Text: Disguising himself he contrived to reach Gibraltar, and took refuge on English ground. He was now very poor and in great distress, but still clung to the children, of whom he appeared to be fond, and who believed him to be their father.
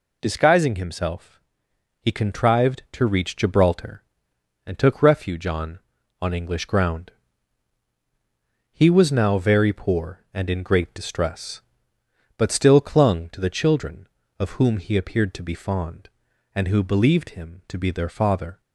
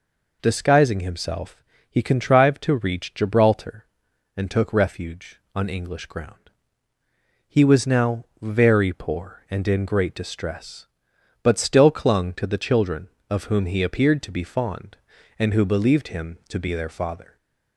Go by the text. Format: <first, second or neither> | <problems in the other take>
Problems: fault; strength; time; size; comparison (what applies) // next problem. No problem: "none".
second | pauses between "himself" and "he"; noticeable; at 1.4 s; 0.62 s long; slight in the second // says "on" twice; at 6.2 s